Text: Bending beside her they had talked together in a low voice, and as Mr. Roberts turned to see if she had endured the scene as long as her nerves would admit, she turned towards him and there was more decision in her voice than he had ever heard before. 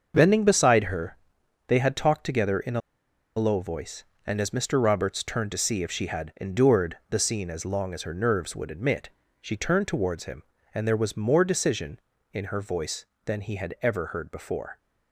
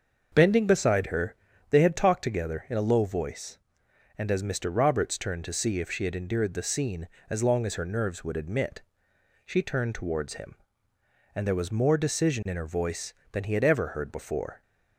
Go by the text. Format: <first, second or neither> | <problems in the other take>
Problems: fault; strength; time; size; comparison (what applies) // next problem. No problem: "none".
second | starts louder than the rest; until 1.1 s; 6.5 dB; also in the second // pauses between "her" and "they"; noticeable; at 1.1 s; 0.50 s long; slight in the second // pauses between "a" and "low"; noticeable; at 2.8 s; 0.56 s long